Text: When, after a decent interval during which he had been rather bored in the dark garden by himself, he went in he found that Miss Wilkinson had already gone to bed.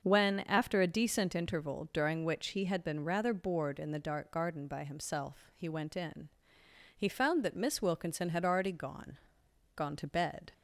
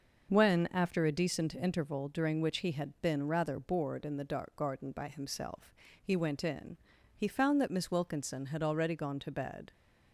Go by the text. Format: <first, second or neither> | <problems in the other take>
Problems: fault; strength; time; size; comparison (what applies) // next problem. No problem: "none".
second | starts louder than the rest; noticeable; until 1.0 s; 6 dB; noticeable in the second // pauses between "in" and "he"; noticeable; at 6.2 s; 0.66 s long; also in the second // says "gone" twice; at 9.7 s